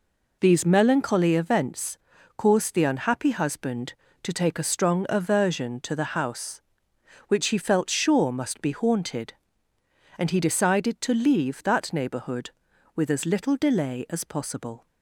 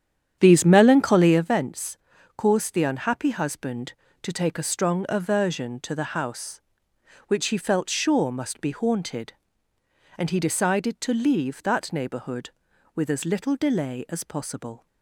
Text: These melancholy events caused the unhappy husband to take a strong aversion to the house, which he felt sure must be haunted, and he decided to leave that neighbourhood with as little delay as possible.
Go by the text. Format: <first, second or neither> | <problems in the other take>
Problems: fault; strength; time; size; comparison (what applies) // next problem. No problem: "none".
first | starts louder than the rest; strong; until 1.6 s; 9 dB // pauses between "events" and "caused"; at 1.9 s; 0.40 s long; also in the first